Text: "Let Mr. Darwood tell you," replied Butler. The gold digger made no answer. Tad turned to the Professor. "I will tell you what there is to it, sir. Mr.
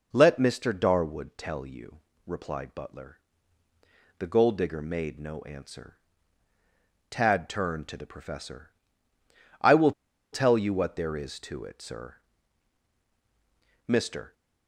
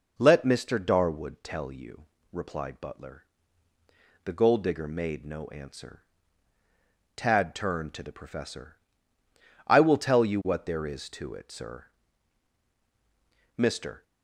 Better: second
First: pauses between "will" and "tell"; at 9.9 s; 0.40 s long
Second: none

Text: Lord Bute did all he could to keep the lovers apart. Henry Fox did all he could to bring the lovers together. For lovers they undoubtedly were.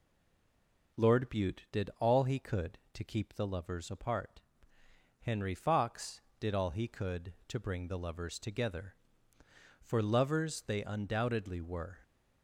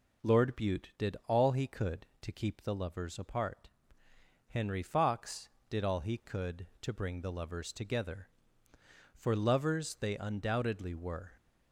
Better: second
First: stays silent before the first word; slight; until 0.9 s; 0.9 s long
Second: none

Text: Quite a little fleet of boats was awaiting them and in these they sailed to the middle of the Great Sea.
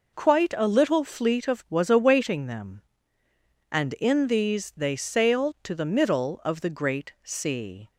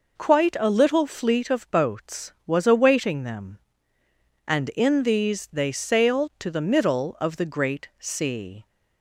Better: second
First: skips "boats"; at 1.6 s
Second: none

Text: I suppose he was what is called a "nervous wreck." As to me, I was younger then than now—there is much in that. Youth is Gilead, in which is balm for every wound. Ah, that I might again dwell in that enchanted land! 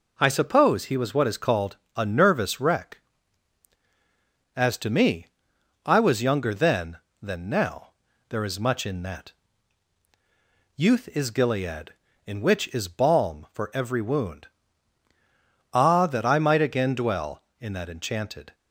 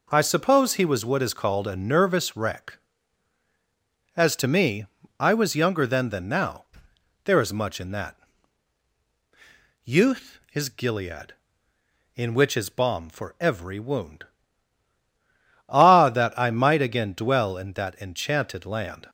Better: second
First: pauses between "called" and "a"; slight; at 1.7 s; 0.18 s long // stops before "land"; at 18.5 s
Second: none

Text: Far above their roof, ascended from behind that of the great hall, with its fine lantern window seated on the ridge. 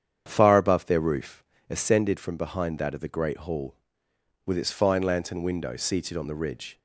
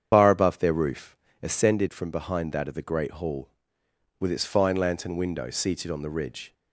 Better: first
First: starts louder than the rest; strong; until 1.2 s; 8.5 dB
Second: loses the start of "Far"; at 0.1 s; 135 ms // starts louder than the rest; strong; until 1.1 s; 8 dB

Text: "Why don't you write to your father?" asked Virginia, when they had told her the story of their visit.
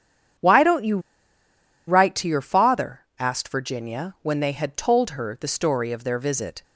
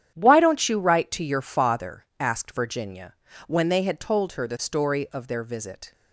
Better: second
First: starts louder than the rest; strong; until 2.2 s; 8.5 dB // pauses between "you" and "write"; noticeable; at 0.9 s; 0.88 s long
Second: starts louder than the rest; strong; until 1.1 s; 10 dB

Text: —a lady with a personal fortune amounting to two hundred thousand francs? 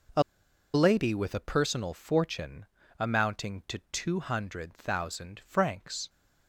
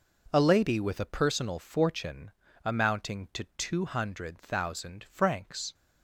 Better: second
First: pauses between "a" and "lady"; noticeable; at 0.2 s; 0.52 s long // pauses between "fortune" and "amounting"; slight; at 2.6 s; 0.34 s long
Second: pauses between "fortune" and "amounting"; slight; at 2.3 s; 0.34 s long

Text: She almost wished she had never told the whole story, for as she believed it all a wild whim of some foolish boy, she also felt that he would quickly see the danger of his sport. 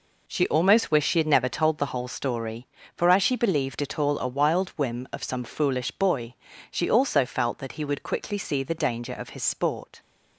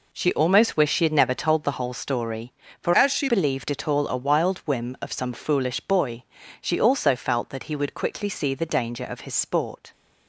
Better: first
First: none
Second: changes voice from "as" to "she"; from 2.9 to 3.2 s; 0.3 s long

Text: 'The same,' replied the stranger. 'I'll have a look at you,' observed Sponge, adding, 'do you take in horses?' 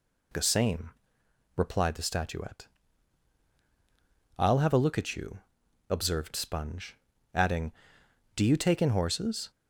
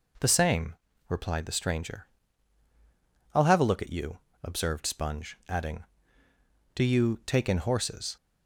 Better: second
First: says "statuette" for "stranger"; at 2.0 s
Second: none

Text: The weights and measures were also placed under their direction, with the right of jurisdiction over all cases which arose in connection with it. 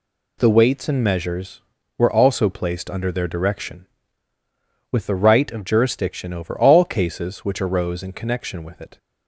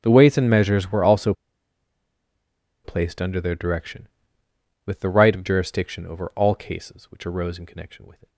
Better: first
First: none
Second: starts louder than the rest; strong; until 1.0 s; 9 dB // pauses between "also" and "placed"; strong; at 1.3 s; 1.5 s long

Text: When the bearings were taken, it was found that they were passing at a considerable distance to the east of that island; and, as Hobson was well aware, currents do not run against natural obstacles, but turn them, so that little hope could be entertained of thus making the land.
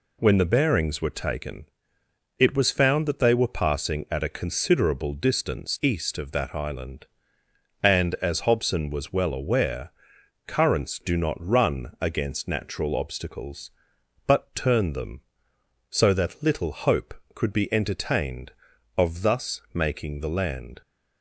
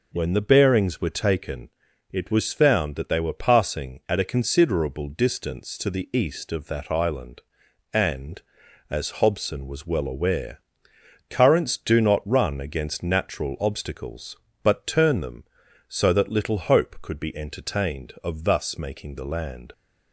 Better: second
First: skips "to the"; at 5.8 s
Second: none

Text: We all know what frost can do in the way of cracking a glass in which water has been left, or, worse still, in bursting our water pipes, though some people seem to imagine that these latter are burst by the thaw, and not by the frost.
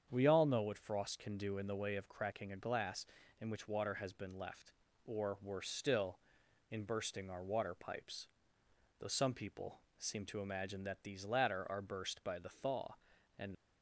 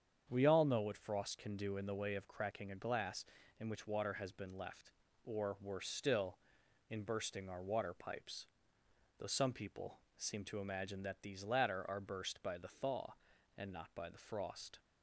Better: second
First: starts louder than the rest; strong; until 1.1 s; 8 dB // pauses between "people" and "seem"; slight; at 9.8 s; 0.17 s long // stops before "not by the frost"; at 13.5 s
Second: starts louder than the rest; strong; until 1.2 s; 8 dB // pauses between "people" and "seem"; slight; at 10.0 s; 0.16 s long

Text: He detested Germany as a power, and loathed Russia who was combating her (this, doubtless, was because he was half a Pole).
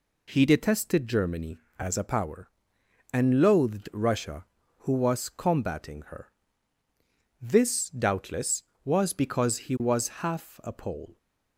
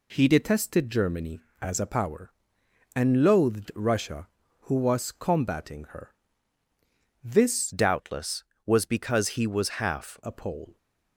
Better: first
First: none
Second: changes voice from "doubtless" to "half"; from 7.7 to 10.2 s; 2.5 s long

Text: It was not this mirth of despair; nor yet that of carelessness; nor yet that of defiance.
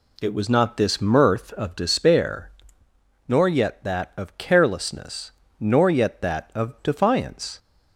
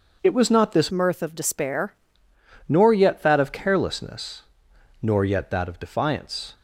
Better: first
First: none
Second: changes voice from "mirth" to "despair"; from 0.9 to 1.9 s; 1.0 s long

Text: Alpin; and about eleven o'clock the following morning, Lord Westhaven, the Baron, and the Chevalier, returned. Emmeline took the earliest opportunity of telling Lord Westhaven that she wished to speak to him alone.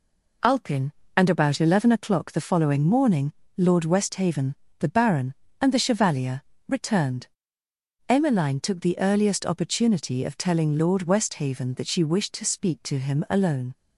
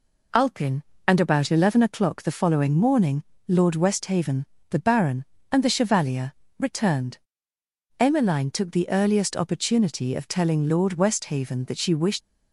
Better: first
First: none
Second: stops before "to speak to him alone"; at 12.2 s

